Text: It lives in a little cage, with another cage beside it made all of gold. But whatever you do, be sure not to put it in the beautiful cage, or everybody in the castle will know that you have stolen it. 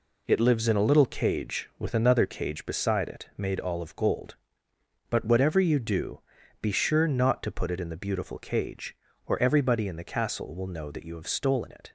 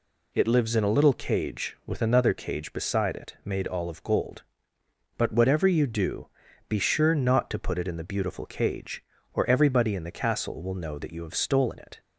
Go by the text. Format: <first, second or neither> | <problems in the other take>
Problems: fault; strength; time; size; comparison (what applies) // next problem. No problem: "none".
second | gets quieter; throughout; 6.5 dB